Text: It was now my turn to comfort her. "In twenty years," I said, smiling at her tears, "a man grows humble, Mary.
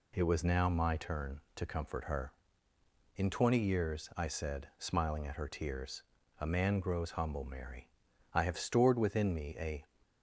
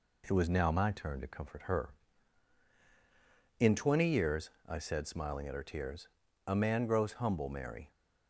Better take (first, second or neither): second